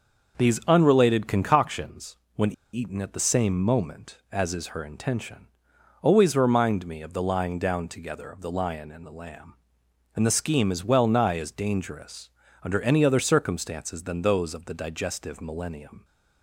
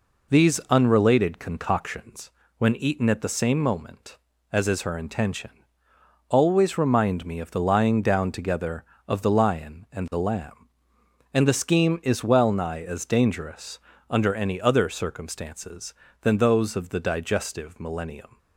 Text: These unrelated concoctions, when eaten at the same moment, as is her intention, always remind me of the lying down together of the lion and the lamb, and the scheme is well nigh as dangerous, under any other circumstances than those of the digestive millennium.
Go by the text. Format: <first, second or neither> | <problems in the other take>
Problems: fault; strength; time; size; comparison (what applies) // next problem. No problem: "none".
second | starts louder than the rest; noticeable; until 1.4 s; 6 dB // pauses between "when" and "eaten"; slight; at 2.5 s; 0.21 s long